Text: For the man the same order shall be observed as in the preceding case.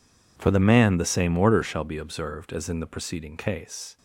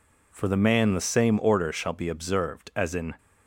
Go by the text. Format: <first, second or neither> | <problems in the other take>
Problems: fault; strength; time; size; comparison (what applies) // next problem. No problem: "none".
first | stops before "the preceding case"; at 3.1 s